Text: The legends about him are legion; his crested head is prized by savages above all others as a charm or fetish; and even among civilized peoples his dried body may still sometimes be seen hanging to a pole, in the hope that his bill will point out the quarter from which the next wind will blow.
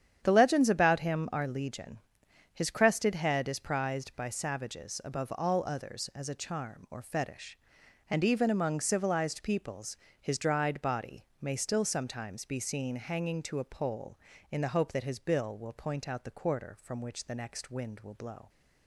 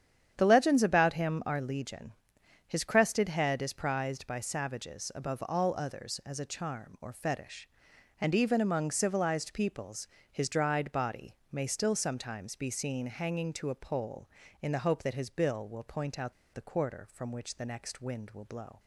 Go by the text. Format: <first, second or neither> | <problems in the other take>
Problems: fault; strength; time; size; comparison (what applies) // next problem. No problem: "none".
first | starts louder than the rest; strong; until 1.3 s; 9 dB; strong in the first // pauses between "peoples" and "his"; slight; at 10.0 s; 0.20 s long; slight in the first // pauses between "body" and "may"; slight; at 11.3 s; 0.16 s long; slight in the first // pauses between "out" and "the"; slight; at 16.3 s; 0.22 s long